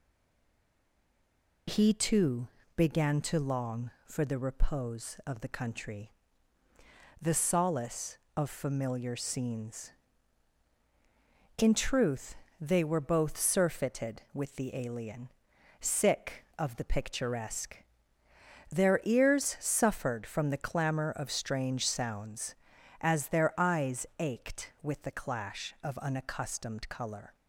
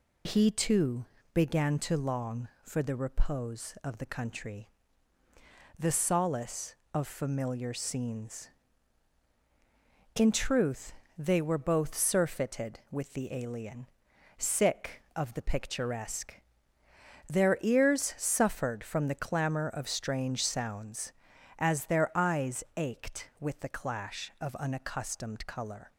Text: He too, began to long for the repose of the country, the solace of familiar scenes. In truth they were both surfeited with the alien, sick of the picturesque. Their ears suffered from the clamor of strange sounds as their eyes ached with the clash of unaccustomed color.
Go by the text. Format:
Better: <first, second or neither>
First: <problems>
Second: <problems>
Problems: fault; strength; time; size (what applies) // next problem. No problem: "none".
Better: second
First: stays silent before the first word; noticeable; until 1.6 s; 1.6 s long // pauses between "truth" and "they"; slight; at 12.3 s; 0.22 s long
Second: pauses between "truth" and "they"; slight; at 10.9 s; 0.22 s long